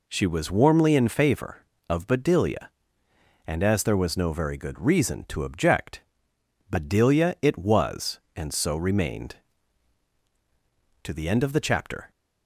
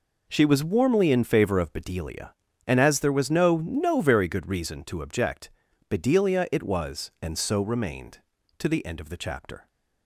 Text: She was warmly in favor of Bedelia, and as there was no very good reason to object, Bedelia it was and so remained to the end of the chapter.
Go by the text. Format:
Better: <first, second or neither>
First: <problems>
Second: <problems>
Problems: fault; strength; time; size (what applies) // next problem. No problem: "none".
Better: first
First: none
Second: says "no" twice; at 3.5 s